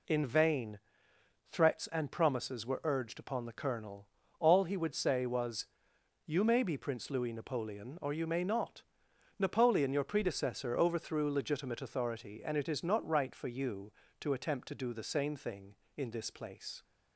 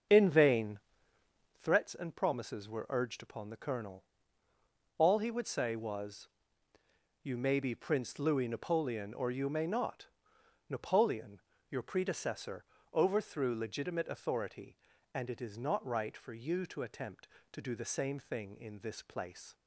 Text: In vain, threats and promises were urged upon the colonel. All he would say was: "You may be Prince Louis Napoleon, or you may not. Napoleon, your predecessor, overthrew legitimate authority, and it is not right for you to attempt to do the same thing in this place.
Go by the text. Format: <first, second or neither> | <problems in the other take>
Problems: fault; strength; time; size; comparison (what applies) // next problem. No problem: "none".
first | starts louder than the rest; until 1.7 s; 7 dB